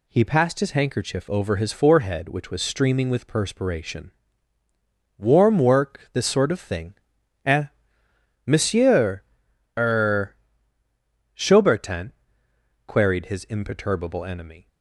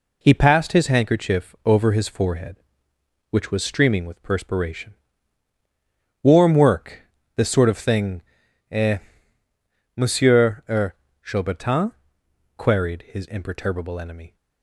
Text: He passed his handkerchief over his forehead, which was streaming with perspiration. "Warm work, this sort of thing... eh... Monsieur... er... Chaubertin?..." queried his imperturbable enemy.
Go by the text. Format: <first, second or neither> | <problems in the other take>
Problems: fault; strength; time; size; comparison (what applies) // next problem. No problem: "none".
first | gets quieter; throughout; 6.5 dB